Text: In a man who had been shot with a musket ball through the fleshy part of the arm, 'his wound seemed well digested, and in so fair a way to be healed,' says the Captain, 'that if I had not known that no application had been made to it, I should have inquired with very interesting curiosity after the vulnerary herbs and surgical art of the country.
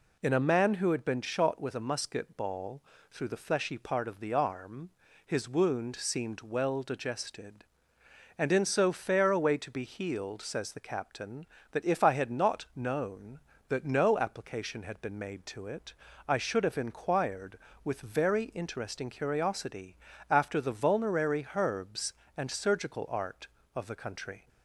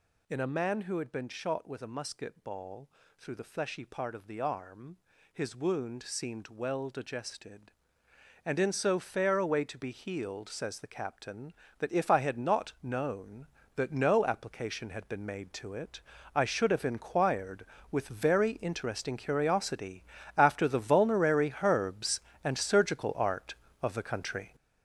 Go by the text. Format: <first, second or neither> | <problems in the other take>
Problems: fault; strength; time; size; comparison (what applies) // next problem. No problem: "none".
first | gets louder; strong; throughout; 9.5 dB // pauses between "ball" and "through"; slight; at 2.8 s; 0.28 s long; slight in the first // pauses between "curiosity" and "after"; slight; at 20.0 s; 0.36 s long; slight in the first